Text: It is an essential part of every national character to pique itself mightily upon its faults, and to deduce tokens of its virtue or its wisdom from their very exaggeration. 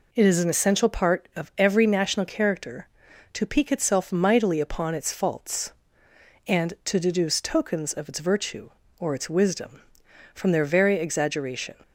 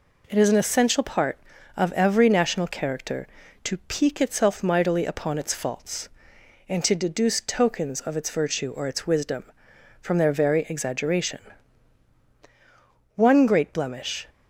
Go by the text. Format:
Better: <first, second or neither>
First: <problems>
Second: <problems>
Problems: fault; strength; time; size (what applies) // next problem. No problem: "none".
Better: first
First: none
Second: goes on to say "One great blemish"; noticeable; from 13.1 s on; 1.1 s long